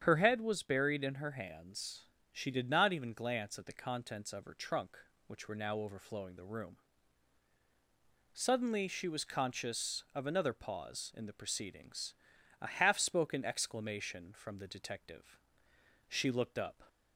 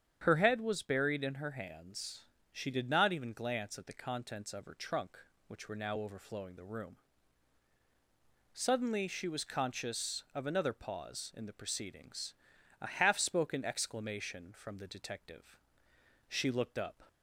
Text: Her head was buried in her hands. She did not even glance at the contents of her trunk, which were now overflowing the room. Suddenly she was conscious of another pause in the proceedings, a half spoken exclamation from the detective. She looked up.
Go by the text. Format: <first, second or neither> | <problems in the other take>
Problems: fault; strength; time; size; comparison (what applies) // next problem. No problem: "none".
neither | starts louder than the rest; strong; the same in both